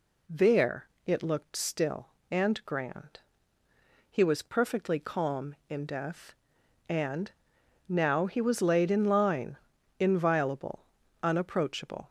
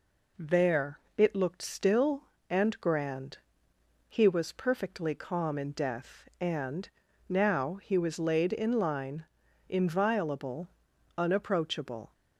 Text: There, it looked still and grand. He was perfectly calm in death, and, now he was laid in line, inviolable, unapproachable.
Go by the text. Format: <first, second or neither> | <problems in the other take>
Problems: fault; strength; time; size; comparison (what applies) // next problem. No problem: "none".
neither | none